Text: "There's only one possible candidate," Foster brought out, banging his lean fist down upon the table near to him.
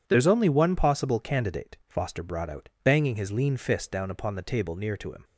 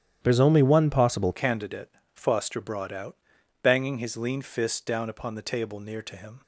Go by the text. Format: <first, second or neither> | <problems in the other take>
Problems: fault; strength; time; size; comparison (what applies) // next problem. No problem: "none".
first | starts louder than the rest; strong; until 1.2 s; 10.5 dB // changes voice at "candidate"; from 1.3 s on; 5.1 s long